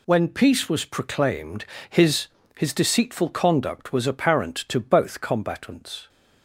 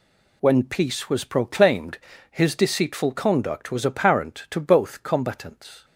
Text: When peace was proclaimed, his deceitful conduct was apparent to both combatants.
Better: second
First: says "his" twice; at 2.5 s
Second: none

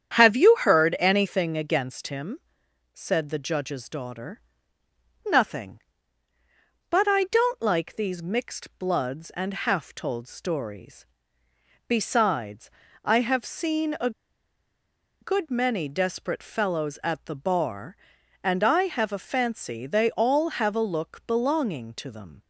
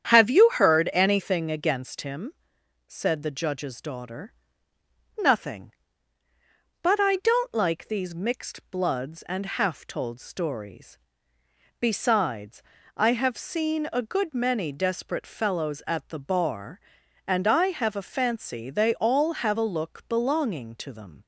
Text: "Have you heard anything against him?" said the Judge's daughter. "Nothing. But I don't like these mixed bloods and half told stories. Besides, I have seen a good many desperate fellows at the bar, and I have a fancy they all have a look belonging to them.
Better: second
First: starts louder than the rest; strong; until 1.2 s; 8.5 dB // pauses between "a" and "good"; at 14.1 s; 1.1 s long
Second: starts louder than the rest; strong; until 1.1 s; 8.5 dB

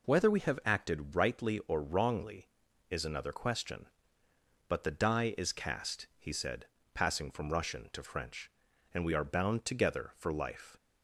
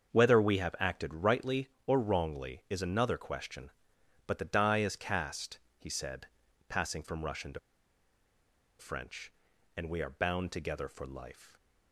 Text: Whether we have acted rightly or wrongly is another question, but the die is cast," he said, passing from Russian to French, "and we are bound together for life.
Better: first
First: none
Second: starts louder than the rest; until 1.1 s; 7 dB // pauses between "to" and "French"; at 7.5 s; 1.2 s long

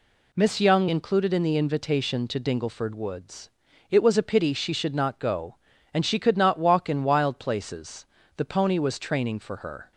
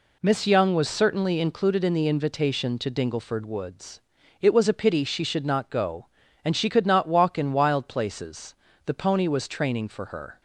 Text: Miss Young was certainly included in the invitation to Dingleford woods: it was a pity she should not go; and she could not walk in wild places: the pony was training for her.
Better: second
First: skips "was certainly"; at 0.8 s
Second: none

